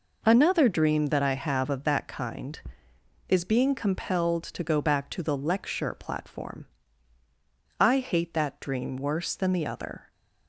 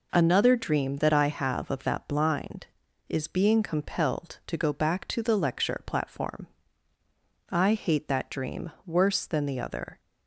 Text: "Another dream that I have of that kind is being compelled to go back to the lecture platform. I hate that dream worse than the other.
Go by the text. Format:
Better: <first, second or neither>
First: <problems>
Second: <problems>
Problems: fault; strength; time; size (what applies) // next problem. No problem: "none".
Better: first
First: none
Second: says "blind" for "kind"; at 2.0 s